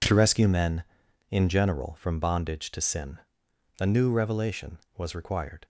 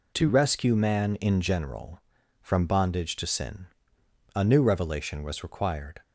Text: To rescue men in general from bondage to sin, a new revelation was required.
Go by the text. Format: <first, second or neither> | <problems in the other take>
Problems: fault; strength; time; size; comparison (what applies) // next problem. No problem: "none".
first | says "man" for "men"; at 0.7 s